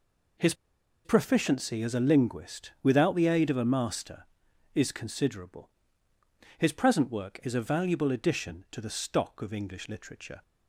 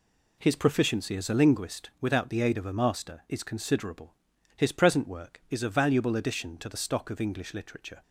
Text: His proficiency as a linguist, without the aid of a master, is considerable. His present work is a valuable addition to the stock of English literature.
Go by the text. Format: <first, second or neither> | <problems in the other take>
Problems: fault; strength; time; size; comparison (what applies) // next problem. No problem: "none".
second | pauses between "His" and "proficiency"; noticeable; at 0.5 s; 0.51 s long